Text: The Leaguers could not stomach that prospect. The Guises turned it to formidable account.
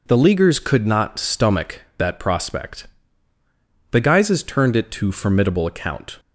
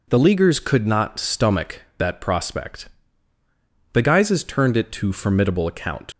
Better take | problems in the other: first | leaves "account" unfinished; at 6.1 s; 80 ms

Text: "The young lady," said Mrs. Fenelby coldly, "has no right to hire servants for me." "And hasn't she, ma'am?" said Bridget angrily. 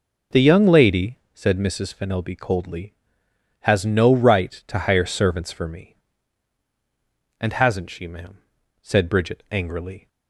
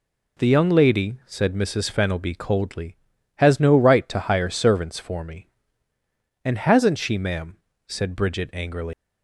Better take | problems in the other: first | leaves "angrily" unfinished; at 8.9 s; 145 ms

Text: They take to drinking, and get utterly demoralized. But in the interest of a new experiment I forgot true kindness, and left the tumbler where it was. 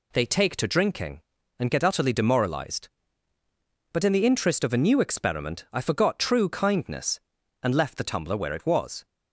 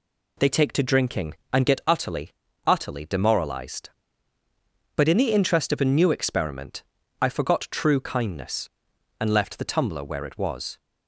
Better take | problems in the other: first | says "utterly" twice; at 2.6 s // pauses between "experiment" and "I"; at 6.8 s; 0.38 s long

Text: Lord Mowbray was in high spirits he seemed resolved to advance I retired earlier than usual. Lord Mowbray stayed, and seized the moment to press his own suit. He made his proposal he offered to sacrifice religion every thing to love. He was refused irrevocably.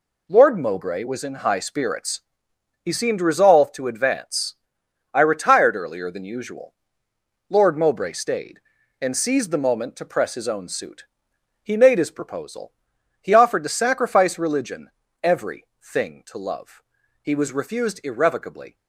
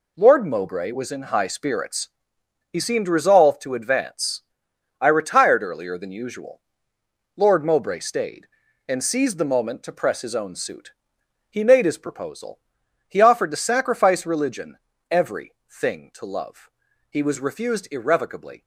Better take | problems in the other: neither | pauses between "spirits" and "he"; noticeable; the same in both // pauses between "advance" and "I"; noticeable; the same in both // pauses between "proposal" and "he"; noticeable; the same in both // pauses between "religion" and "every"; slight; the same in both // pauses between "every" and "thing"; slight; the same in both

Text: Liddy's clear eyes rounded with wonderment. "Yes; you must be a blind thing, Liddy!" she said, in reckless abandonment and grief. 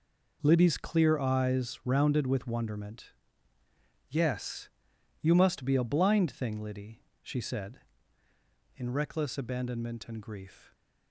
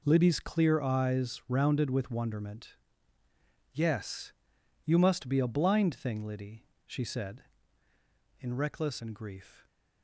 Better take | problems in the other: first | skips "abandonment"; at 9.0 s

